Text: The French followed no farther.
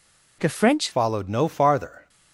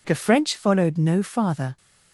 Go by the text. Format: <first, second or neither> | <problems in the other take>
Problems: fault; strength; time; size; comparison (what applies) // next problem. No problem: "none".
second | changes voice at "followed"; from 0.9 s on; 1.1 s long